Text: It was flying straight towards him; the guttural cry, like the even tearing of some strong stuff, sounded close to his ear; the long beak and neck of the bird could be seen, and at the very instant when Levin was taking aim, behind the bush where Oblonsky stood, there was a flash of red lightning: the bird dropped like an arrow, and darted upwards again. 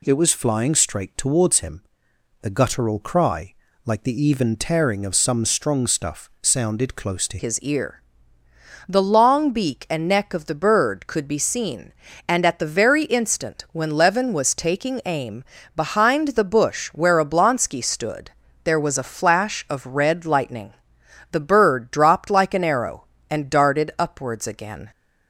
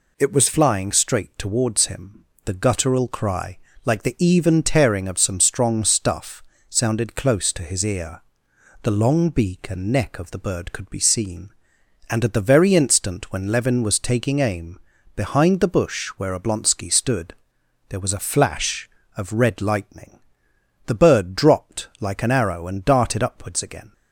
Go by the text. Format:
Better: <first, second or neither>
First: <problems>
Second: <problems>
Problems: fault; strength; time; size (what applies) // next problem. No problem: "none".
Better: second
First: changes voice at "his"; from 7.3 s on; 17.6 s long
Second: none